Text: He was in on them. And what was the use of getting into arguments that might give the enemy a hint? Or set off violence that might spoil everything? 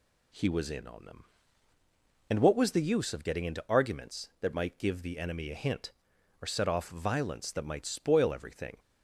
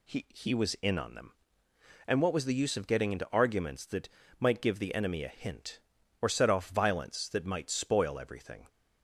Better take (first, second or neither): first